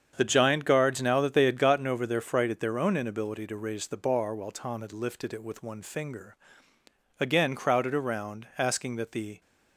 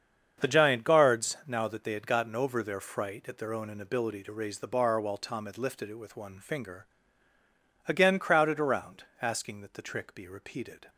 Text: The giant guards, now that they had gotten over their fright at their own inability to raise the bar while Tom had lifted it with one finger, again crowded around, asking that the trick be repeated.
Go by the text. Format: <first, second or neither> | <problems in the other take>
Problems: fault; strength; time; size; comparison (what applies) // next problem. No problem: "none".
second | starts louder than the rest; strong; until 1.1 s; 7.5 dB; strong in the second // stops before "trick be repeated"; at 9.4 s